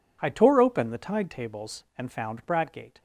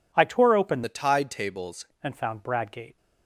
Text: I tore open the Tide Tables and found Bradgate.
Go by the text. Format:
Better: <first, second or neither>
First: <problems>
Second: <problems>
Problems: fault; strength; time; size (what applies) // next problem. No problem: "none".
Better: first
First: none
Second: changes voice from "the" to "Tables"; from 0.8 to 1.8 s; 1.0 s long